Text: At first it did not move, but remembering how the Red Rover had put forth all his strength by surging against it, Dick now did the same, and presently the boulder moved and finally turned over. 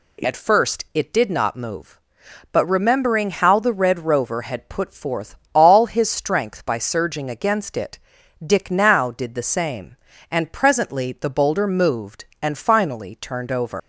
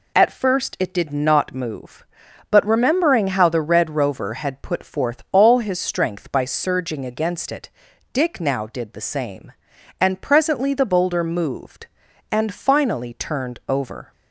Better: second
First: pauses between "forth" and "all"; slight; at 5.3 s; 0.18 s long // leaves "over" unfinished; at 13.7 s; 135 ms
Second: none

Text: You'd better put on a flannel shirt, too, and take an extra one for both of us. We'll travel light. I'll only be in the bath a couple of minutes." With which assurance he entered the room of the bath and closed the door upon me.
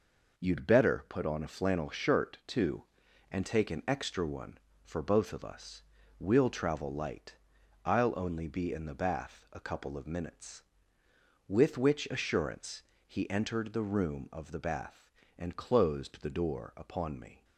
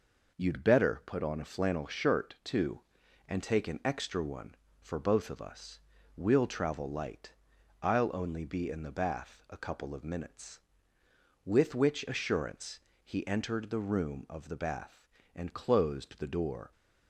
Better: first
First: pauses between "assurance" and "he"; slight; at 12.8 s; 0.24 s long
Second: pauses between "assurance" and "he"; slight; at 12.7 s; 0.24 s long // stops before "upon me"; at 16.7 s

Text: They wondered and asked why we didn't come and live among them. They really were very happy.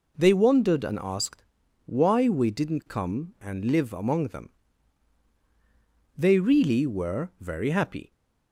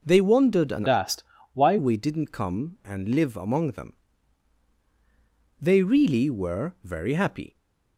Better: first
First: pauses between "asked" and "why"; at 1.4 s; 0.40 s long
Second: changes voice from "asked" to "why"; from 0.8 to 1.7 s; 0.9 s long // pauses between "asked" and "why"; slight; at 1.2 s; 0.30 s long

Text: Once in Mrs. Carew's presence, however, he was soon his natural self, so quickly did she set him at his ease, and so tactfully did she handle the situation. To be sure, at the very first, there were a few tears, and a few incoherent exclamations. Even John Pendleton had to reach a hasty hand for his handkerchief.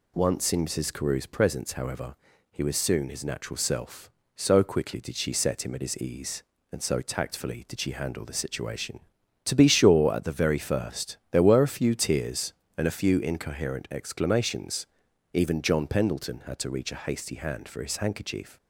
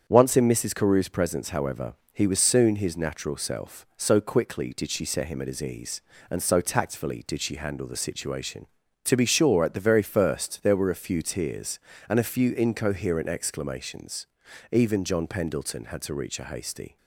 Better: first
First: none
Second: starts louder than the rest; strong; until 1.0 s; 7.5 dB // stops before "hand for his handkerchief"; at 16.9 s

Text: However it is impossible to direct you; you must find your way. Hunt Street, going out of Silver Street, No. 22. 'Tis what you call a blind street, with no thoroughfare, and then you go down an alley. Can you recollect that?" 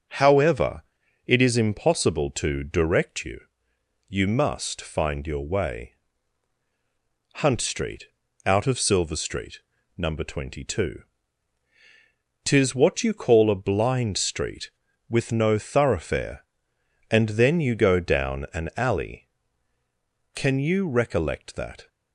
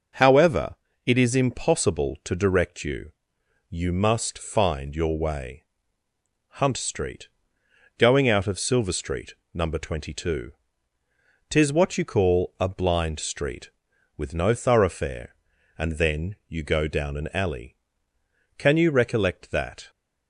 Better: second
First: starts louder than the rest; until 1.5 s; 6 dB // pauses between "However" and "it"; at 0.8 s; 0.44 s long // skips "going"; at 8.2 s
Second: pauses between "However" and "it"; slight; at 0.7 s; 0.30 s long

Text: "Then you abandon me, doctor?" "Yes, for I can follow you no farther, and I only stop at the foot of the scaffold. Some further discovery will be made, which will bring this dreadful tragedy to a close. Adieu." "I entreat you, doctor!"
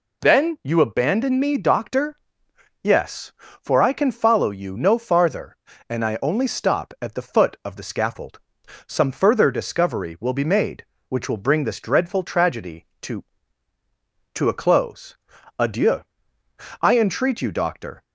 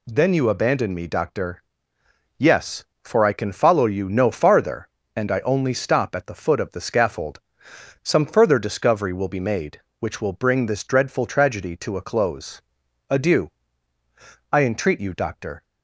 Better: second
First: says "to" twice; at 14.3 s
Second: none

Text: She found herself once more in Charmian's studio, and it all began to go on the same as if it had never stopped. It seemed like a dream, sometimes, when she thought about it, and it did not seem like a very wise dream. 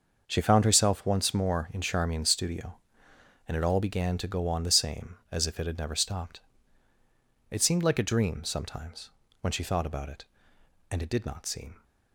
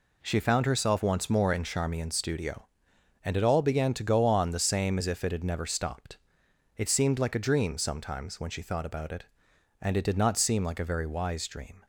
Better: second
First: starts louder than the rest; noticeable; until 1.2 s; 6 dB // stops before "like a very wise dream"; at 11.8 s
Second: none

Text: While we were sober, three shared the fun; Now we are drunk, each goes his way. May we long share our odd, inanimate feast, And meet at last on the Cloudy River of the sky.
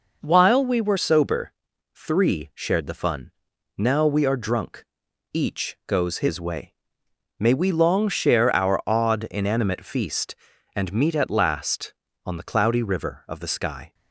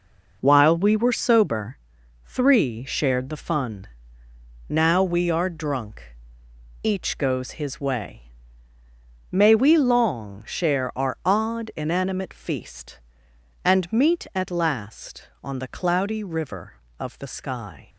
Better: second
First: changes voice at "sober"; from 0.9 s on; 13.0 s long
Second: none

